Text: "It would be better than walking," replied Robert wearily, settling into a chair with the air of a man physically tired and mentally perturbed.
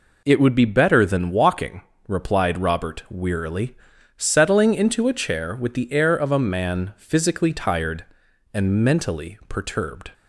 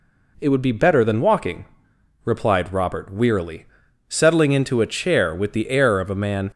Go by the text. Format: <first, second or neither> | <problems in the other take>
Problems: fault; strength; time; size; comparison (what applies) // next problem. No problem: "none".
first | stops before "physically tired and mentally perturbed"; at 6.5 s